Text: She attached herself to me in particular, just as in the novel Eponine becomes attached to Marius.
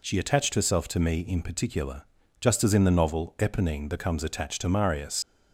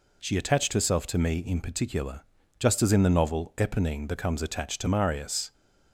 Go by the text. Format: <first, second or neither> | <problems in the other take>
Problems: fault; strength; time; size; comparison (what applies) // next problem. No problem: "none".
second | leaves "Marius" unfinished; at 5.2 s; 120 ms